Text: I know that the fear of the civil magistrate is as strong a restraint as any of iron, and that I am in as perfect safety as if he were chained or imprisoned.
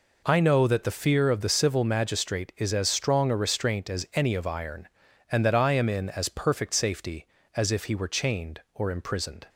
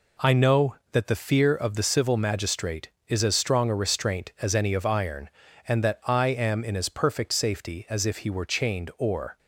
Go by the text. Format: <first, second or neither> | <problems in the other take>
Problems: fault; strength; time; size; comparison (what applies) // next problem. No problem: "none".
first | stops before "imprisoned"; at 9.3 s